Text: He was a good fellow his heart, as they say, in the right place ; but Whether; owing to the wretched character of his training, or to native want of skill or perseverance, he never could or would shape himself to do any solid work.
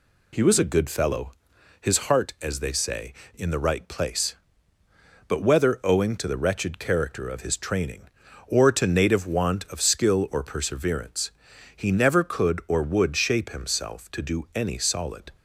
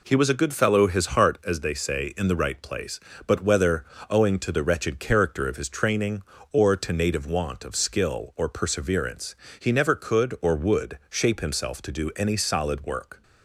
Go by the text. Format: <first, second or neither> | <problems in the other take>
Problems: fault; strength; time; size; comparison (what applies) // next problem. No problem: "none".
second | pauses between "fellow" and "his"; noticeable; at 1.2 s; 0.50 s long // stops before "work"; at 15.3 s